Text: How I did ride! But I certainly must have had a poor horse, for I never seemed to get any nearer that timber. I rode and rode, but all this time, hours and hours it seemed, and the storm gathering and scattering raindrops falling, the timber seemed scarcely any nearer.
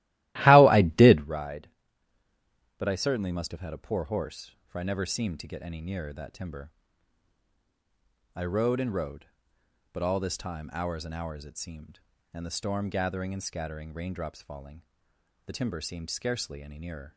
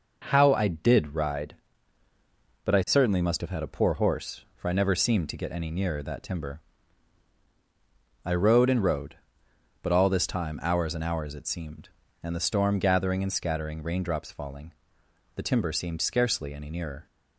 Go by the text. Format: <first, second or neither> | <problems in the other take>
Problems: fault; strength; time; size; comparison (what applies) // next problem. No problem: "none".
second | starts louder than the rest; strong; until 1.3 s; 16.5 dB